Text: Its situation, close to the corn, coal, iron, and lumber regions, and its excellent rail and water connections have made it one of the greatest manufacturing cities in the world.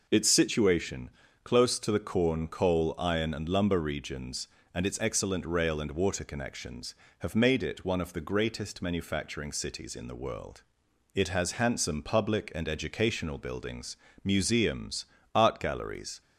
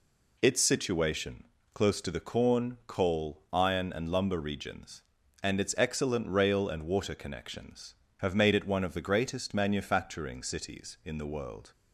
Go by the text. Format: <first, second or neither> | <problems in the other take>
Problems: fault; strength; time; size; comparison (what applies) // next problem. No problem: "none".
second | goes on to say "It has handsome public and educational buildings museums art galleries"; strong; from 11.1 s on; 5.0 s long